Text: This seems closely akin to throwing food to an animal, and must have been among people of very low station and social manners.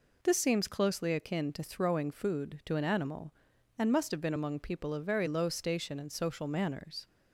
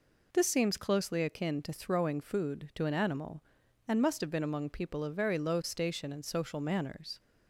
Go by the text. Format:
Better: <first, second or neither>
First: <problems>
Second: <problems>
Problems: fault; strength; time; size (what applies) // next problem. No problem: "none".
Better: neither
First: none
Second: none